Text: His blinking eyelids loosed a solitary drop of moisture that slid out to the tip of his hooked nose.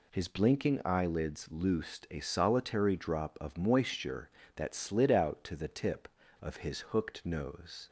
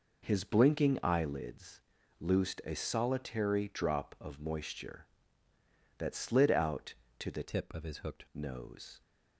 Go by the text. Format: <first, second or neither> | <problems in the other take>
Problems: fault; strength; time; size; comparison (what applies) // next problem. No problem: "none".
first | pauses between "eyelids" and "loosed"; slight; at 1.8 s; 0.36 s long // changes voice from "tip" to "hooked"; from 7.4 to 8.2 s; 0.8 s long